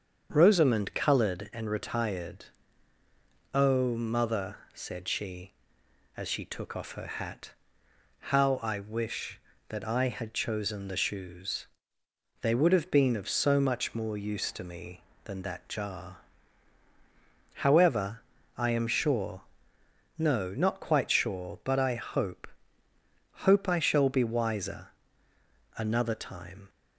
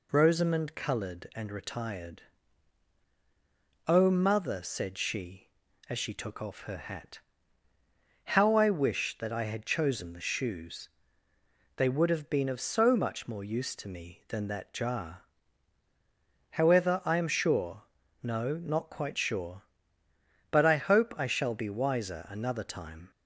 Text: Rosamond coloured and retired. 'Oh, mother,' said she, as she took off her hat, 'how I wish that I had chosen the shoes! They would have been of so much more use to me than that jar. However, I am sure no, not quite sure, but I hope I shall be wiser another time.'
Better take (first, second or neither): second